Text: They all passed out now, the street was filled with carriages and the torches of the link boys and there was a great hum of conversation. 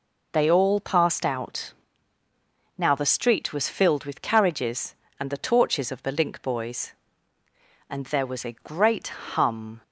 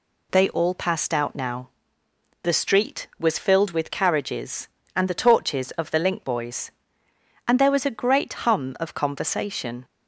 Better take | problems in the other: second | pauses between "out" and "now"; at 1.7 s; 1.0 s long // stops before "of conversation"; at 9.8 s

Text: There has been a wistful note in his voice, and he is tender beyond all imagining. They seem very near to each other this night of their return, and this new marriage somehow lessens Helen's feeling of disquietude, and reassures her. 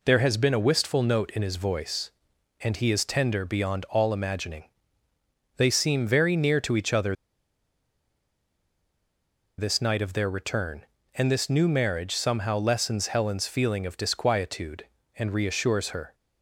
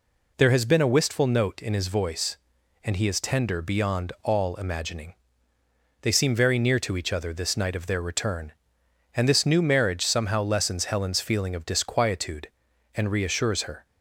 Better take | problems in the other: second | pauses between "other" and "this"; strong; at 7.1 s; 2.4 s long

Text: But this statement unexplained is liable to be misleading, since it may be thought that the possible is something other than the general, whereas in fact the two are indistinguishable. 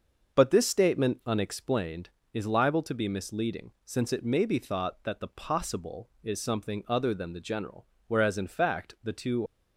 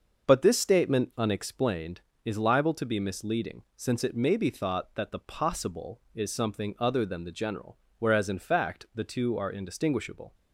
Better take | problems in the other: second | starts louder than the rest; until 1.4 s; 6.5 dB; also in the second // stops before "are indistinguishable"; at 9.4 s

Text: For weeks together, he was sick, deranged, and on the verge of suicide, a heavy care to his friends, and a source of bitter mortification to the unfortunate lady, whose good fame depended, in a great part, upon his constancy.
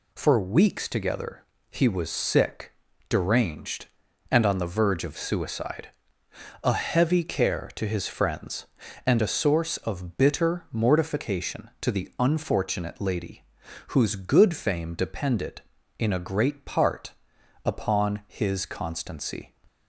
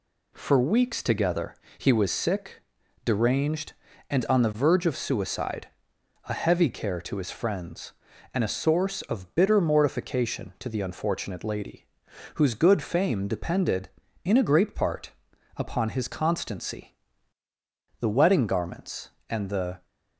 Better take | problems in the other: first | goes on to say "The wedding garments and the"; strong; from 18.0 s on; 1.8 s long

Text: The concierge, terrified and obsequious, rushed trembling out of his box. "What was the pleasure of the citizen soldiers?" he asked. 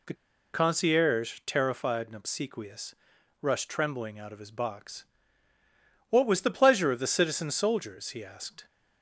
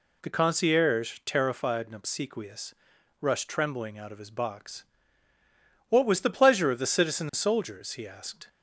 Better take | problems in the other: second | pauses between "The" and "concierge"; at 0.1 s; 0.38 s long

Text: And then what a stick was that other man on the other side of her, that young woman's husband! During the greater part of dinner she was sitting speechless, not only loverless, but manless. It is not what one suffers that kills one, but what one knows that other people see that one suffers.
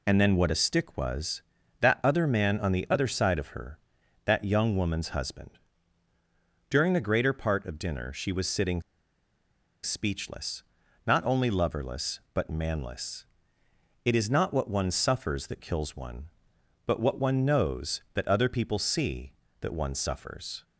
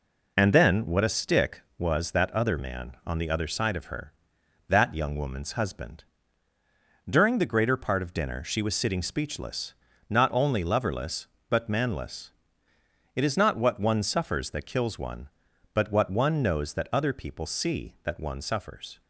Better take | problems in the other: second | pauses between "sitting" and "speechless"; at 8.8 s; 1.0 s long

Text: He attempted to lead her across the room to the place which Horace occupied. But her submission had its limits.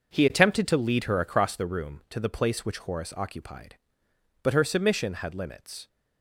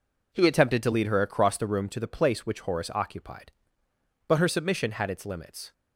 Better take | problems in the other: second | skips "its"; at 5.3 s

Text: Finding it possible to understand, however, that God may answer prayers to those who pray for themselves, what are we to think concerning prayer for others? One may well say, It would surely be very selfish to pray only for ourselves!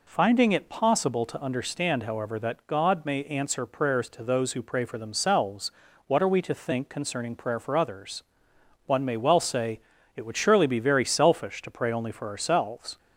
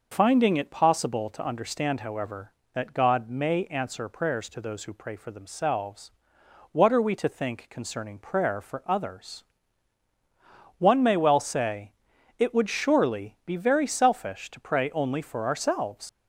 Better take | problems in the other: first | leaves "ourselves" unfinished; at 16.0 s; 90 ms

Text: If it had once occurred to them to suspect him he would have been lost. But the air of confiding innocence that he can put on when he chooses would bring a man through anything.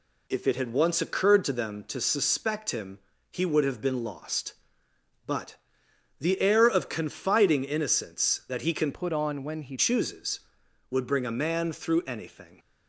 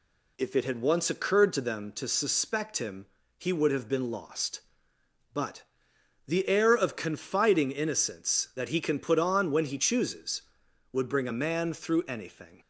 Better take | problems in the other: second | pauses between "him" and "he"; slight; at 2.9 s; 0.32 s long; slight in the second // pauses between "But" and "the"; noticeable; at 5.5 s; 0.64 s long; noticeable in the second // changes voice from "put" to "he"; from 8.9 to 9.7 s; 0.8 s long

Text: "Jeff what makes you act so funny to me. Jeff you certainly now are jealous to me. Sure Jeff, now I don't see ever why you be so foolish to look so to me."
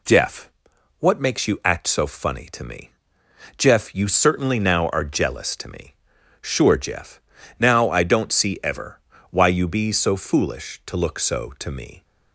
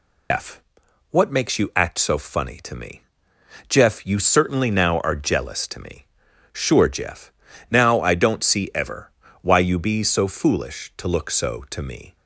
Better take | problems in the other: first | loses the start of "Jeff"; at 0.3 s; 150 ms // pauses between "Jeff" and "what"; noticeable; at 0.6 s; 0.50 s long; noticeable in the first // pauses between "ever" and "why"; slight; at 9.1 s; 0.30 s long; slight in the first

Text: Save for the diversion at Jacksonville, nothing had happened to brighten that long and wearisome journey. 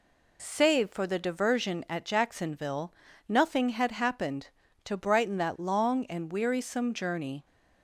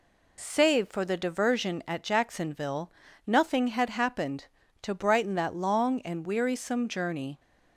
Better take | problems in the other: neither | none

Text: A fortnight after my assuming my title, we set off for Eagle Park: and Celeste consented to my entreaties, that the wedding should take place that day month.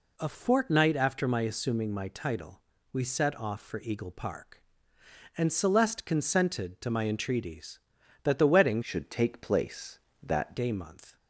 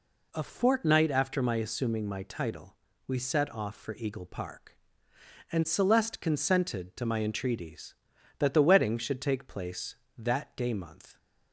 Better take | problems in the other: second | changes voice from "should" to "that"; from 8.8 to 10.5 s; 1.7 s long

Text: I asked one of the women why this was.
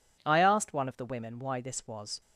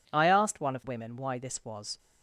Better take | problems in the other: first | skips "the"; at 0.8 s

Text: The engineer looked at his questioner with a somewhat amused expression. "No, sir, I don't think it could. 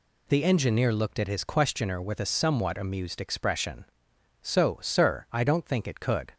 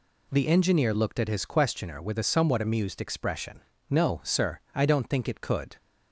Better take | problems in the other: second | says "So" for "No"; at 4.4 s

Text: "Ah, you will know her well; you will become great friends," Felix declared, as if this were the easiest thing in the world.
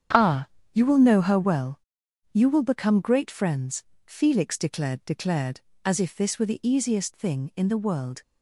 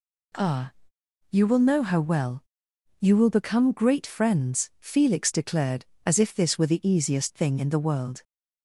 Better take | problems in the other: second | starts louder than the rest; strong; until 1.4 s; 8.5 dB // says "declared" twice; at 5.0 s

